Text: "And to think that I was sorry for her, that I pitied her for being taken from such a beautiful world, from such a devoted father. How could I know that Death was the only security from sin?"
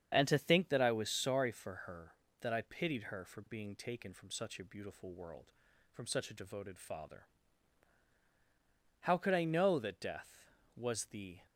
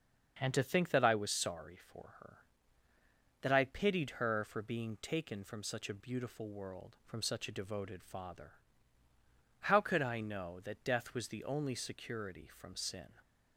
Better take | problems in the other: second | starts louder than the rest; strong; until 1.1 s; 8 dB; also in the second // stops before "only security from sin"; at 11.4 s

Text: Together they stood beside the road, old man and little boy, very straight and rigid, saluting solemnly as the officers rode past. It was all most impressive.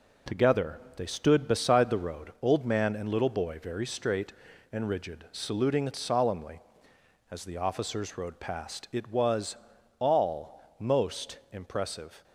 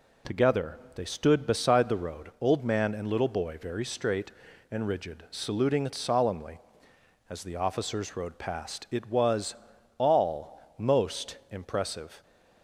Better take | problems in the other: second | gets quieter; throughout; 7 dB // pauses between "Together" and "they"; slight; at 0.8 s; 0.16 s long; slight in the second // pauses between "was" and "all"; at 9.5 s; 0.44 s long; also in the second

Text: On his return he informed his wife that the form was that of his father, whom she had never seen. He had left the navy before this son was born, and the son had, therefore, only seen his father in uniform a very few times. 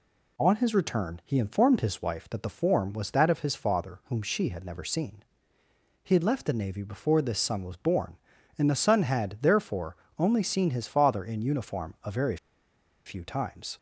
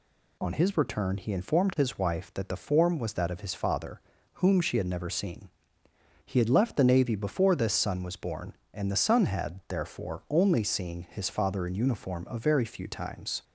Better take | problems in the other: second | pauses between "very" and "few"; noticeable; at 12.3 s; 0.69 s long

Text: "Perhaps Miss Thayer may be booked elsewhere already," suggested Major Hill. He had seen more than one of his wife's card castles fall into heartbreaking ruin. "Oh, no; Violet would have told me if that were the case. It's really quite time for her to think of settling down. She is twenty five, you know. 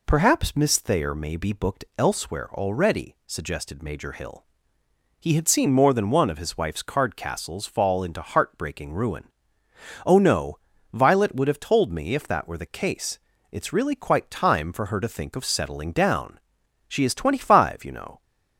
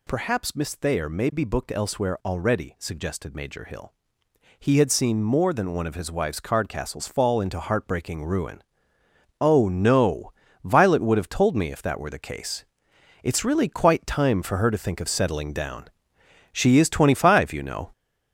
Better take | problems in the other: first | gets louder; noticeable; throughout; 5.5 dB

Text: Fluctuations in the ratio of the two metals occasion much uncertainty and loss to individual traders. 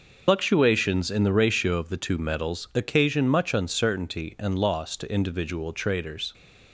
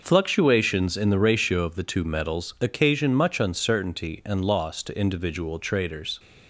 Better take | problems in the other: second | loses the start of "Fluctuations"; at 0.2 s; 110 ms

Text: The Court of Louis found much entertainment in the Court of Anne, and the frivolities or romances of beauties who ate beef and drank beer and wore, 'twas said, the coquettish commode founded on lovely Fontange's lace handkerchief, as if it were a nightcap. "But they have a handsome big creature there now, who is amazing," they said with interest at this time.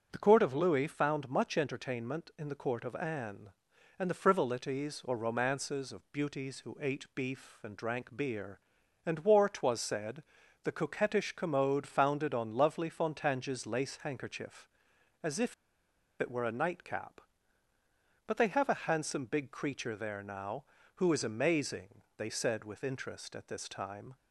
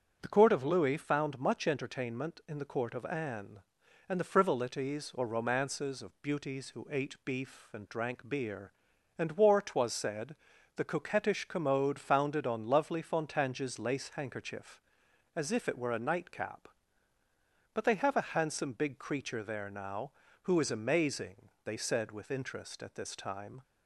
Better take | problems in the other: second | starts louder than the rest; strong; until 1.1 s; 7.5 dB; strong in the second // pauses between "if" and "it"; noticeable; at 15.5 s; 0.66 s long

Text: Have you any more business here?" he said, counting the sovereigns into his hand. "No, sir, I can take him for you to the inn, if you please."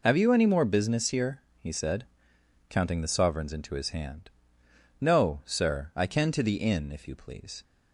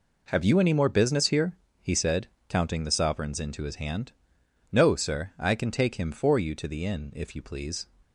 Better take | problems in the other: second | skips "take him for you"; at 6.3 s

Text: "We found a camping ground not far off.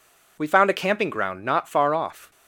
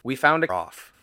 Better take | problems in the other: first | skips "camping ground not far"; at 0.4 s

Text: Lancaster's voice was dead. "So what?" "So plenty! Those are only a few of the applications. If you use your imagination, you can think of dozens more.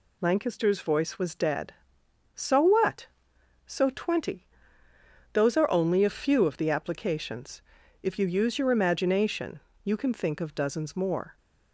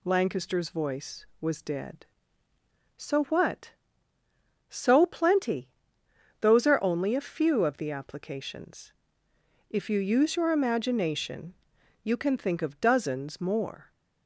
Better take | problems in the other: second | says "twenty" for "plenty"; at 3.8 s

